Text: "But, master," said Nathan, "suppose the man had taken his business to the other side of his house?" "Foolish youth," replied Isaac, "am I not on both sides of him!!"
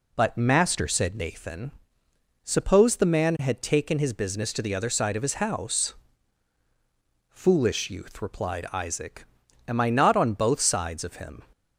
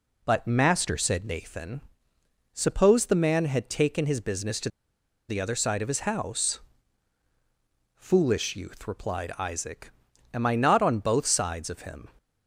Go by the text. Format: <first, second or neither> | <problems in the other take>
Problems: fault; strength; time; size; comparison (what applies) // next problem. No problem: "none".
first | pauses between "to" and "the"; noticeable; at 4.6 s; 0.60 s long